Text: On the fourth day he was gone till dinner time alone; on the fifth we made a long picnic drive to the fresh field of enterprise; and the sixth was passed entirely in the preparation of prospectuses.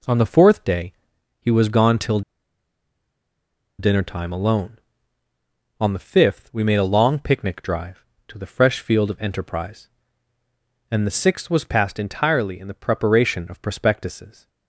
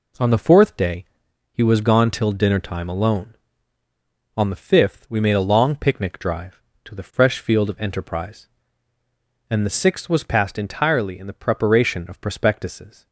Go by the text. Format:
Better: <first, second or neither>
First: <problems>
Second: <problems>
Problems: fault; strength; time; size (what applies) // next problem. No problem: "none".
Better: second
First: pauses between "day" and "he"; noticeable; at 0.9 s; 0.48 s long // pauses between "till" and "dinner"; strong; at 2.2 s; 1.5 s long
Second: pauses between "day" and "he"; noticeable; at 1.0 s; 0.48 s long